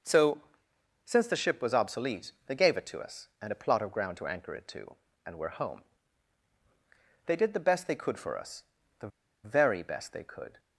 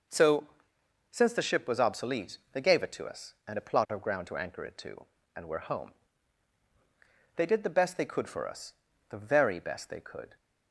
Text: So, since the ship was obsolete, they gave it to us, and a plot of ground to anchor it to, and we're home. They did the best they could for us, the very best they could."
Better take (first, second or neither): second